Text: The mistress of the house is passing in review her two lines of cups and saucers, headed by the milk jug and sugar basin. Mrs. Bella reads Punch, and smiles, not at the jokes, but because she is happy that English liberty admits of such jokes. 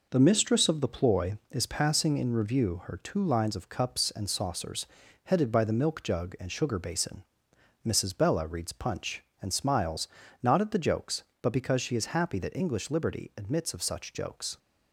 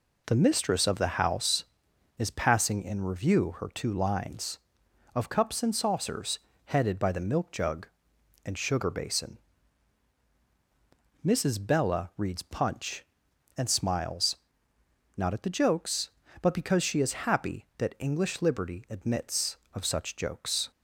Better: second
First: says "ploy" for "house"; at 0.8 s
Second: none

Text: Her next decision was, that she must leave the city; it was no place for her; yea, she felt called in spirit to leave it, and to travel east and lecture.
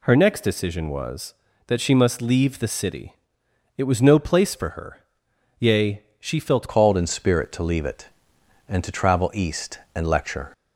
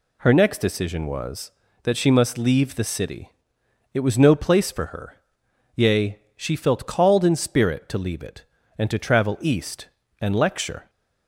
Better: second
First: changes voice at "called"; from 6.6 s on; 3.9 s long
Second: none

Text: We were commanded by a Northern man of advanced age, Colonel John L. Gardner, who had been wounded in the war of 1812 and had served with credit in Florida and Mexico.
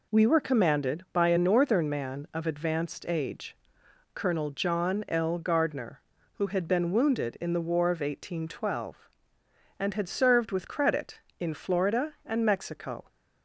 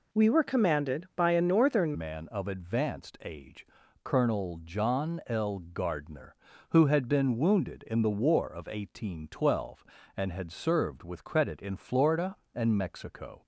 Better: first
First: none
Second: changes voice at "man"; from 1.9 s on; 11.5 s long

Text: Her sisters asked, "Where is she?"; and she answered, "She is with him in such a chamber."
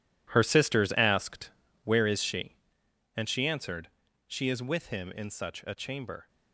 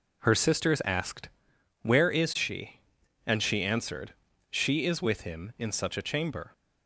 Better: second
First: gets quieter; strong; throughout; 13 dB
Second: none

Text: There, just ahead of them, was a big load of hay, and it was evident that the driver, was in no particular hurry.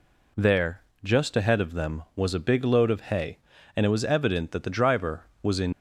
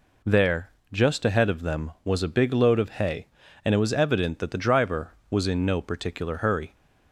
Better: second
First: stops before "no particular hurry"; at 5.7 s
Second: none

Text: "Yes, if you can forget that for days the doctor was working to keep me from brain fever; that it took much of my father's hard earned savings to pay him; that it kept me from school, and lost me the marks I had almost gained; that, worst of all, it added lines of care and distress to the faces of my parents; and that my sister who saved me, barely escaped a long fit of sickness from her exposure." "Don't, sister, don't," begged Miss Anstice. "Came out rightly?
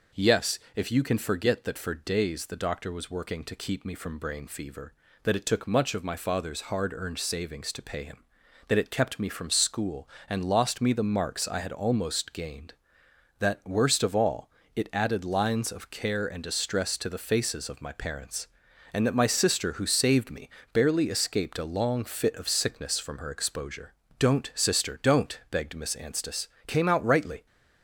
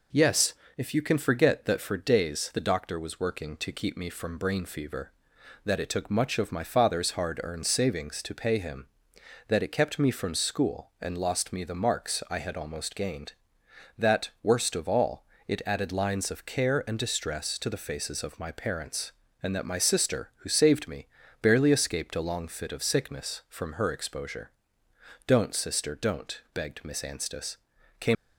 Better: first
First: none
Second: stops before "out rightly"; at 28.1 s

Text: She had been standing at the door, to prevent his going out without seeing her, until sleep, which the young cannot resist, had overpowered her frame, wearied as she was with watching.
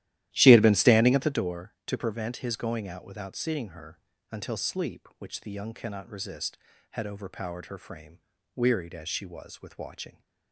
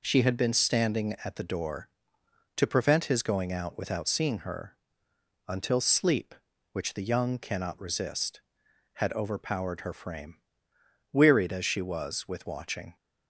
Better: second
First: starts louder than the rest; strong; until 1.5 s; 13.5 dB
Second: none

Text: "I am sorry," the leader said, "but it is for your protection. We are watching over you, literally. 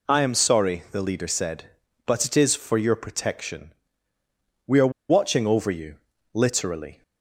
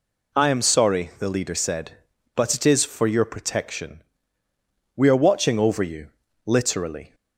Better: second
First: pauses between "are" and "watching"; slight; at 4.9 s; 0.19 s long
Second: none

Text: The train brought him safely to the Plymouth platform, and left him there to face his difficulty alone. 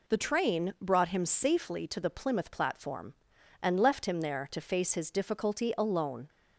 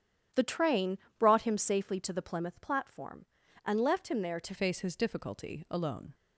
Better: first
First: none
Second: starts louder than the rest; strong; until 1.5 s; 10 dB // pauses between "train" and "brought"; slight; at 0.9 s; 0.22 s long // changes voice at "face"; from 4.5 s on; 1.6 s long

